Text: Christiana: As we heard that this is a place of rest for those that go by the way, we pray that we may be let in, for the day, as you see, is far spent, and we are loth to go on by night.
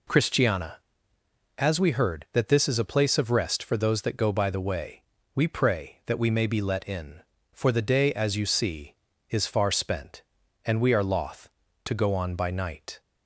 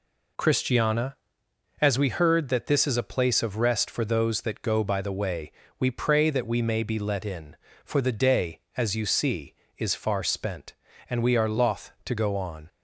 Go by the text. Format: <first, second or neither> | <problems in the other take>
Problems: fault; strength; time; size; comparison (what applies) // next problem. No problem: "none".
first | stops before "by night"; at 12.6 s